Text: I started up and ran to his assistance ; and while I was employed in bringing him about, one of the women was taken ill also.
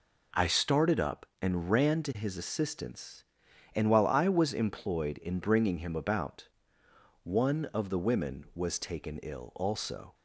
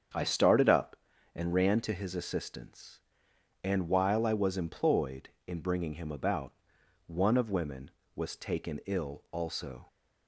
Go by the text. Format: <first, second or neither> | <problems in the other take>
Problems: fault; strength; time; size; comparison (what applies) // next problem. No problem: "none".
first | starts louder than the rest; strong; until 1.5 s; 7.5 dB // skips "the"; at 7.5 s